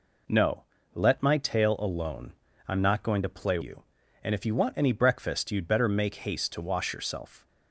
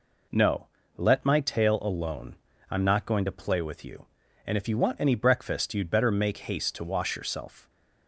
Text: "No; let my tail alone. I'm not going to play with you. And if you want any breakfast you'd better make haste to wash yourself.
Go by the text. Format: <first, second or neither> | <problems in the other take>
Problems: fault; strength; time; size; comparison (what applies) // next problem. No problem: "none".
second | skips "with"; at 3.6 s